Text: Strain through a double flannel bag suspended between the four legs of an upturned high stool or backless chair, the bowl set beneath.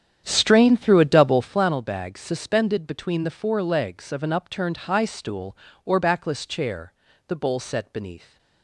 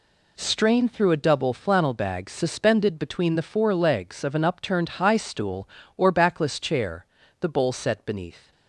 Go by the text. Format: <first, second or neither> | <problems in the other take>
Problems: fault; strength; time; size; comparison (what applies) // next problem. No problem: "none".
second | starts louder than the rest; strong; until 1.7 s; 9 dB